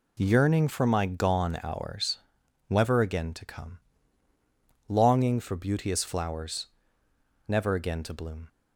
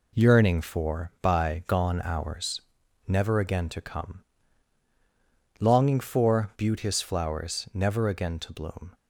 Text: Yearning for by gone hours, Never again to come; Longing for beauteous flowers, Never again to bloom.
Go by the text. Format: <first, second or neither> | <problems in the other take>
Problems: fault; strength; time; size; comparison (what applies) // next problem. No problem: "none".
second | says "my" for "by"; at 0.8 s